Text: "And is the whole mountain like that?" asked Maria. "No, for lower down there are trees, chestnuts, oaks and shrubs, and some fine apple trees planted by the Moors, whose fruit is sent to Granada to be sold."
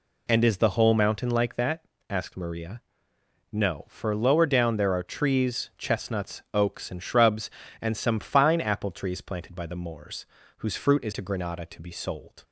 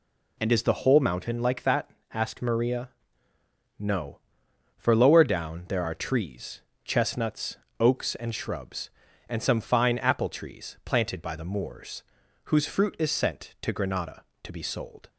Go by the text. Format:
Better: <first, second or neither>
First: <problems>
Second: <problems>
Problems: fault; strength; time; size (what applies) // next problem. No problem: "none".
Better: second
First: skips "sent"; at 11.1 s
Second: none